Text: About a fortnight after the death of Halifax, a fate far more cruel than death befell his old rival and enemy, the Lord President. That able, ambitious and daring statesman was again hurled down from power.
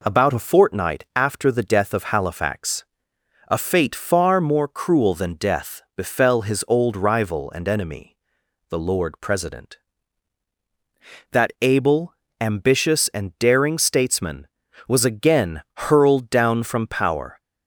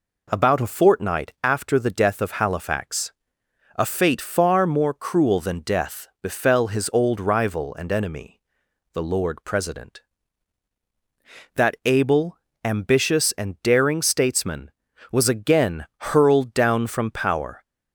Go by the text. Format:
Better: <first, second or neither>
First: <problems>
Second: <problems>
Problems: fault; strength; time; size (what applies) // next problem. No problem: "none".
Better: neither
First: none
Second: none